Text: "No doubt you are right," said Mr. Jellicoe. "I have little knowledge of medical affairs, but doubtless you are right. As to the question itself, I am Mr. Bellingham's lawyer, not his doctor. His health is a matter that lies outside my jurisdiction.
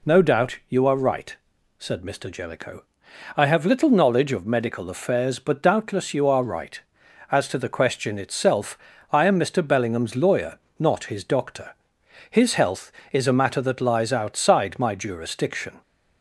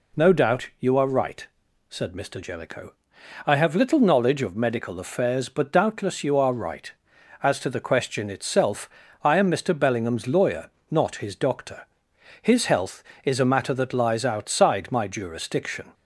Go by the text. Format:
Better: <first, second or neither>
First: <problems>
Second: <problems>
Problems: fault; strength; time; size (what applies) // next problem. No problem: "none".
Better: neither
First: none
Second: none